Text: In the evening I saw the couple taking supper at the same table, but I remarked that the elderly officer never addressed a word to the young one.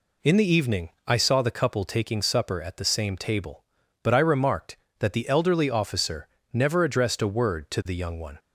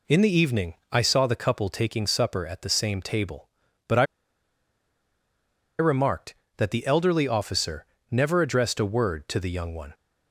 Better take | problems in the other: first | pauses between "evening" and "I"; slight; at 0.7 s; 0.16 s long; slight in the first // pauses between "I" and "remarked"; strong; at 4.0 s; 1.7 s long // pauses between "officer" and "never"; slight; at 7.8 s; 0.24 s long; slight in the first

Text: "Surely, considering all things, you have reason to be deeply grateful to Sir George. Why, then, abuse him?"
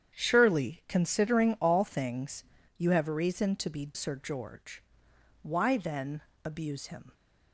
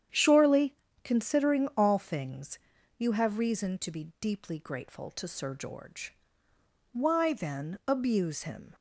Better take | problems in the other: second | starts louder than the rest; strong; until 1.1 s; 8.5 dB; strong in the second // skips "deeply grateful to"; at 3.9 s

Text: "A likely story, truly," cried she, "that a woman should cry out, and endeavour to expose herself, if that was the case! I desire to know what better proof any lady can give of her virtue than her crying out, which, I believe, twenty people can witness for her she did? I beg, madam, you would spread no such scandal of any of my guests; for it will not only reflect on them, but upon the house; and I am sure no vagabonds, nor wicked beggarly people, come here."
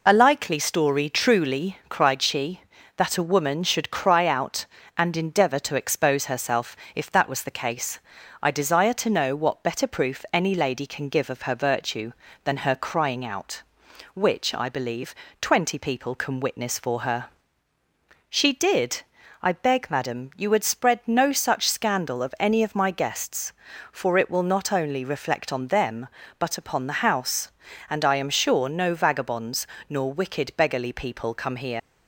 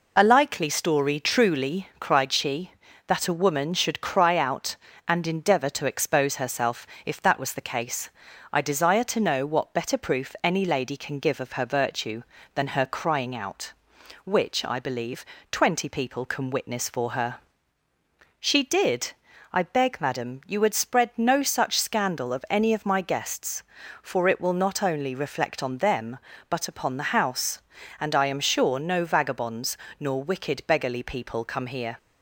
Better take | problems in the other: second | pauses between "her" and "she"; at 17.2 s; 1.0 s long; also in the second // leaves "here" unfinished; at 31.7 s; 65 ms

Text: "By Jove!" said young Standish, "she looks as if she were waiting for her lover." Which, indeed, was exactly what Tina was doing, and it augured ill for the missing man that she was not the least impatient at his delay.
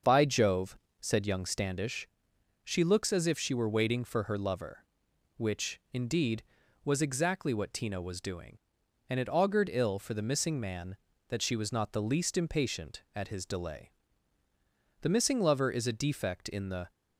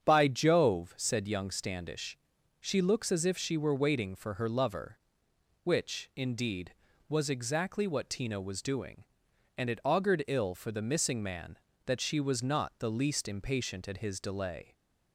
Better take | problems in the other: second | starts louder than the rest; until 1.2 s; 6.5 dB; strong in the second // goes on to say "The missing lover is a defect in the"; strong; from 15.0 s on; 1.9 s long

